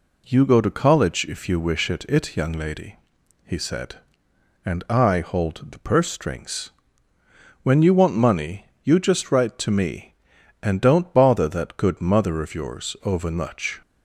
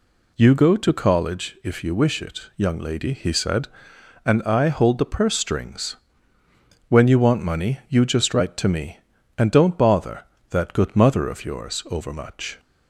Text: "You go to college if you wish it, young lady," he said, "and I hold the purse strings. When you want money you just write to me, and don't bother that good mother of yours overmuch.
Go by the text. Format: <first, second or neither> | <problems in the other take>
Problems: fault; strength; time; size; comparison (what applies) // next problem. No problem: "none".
second | says "it" twice; at 2.0 s // pauses between "money" and "you"; slight; at 8.6 s; 0.16 s long